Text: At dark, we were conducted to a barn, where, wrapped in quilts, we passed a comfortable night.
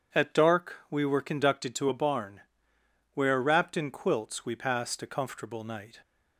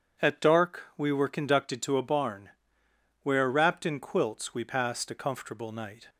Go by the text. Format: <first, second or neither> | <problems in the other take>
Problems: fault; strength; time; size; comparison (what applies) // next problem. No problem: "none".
neither | none